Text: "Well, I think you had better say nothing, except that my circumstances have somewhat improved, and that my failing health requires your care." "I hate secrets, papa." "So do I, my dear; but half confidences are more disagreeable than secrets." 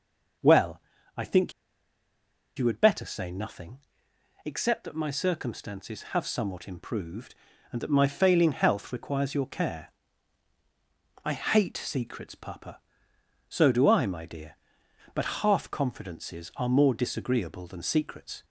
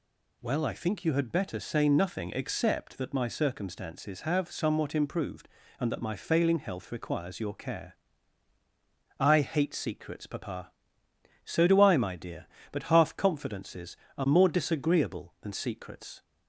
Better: second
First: pauses between "think" and "you"; at 1.5 s; 1.0 s long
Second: none

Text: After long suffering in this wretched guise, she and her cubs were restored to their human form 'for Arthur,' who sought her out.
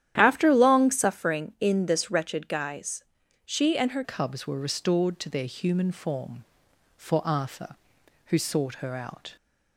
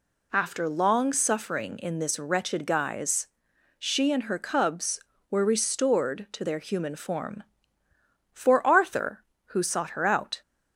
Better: second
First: starts louder than the rest; strong; until 1.1 s; 11 dB // changes voice at "cubs"; from 4.0 s on; 5.3 s long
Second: none

